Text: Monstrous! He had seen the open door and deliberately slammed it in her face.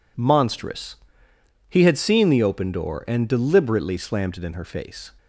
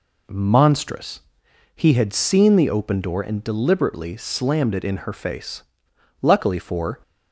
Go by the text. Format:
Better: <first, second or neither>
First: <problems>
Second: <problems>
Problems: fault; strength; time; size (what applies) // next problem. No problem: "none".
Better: first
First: none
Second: goes on to say "Luckily for"; noticeable; from 6.2 s on; 0.78 s long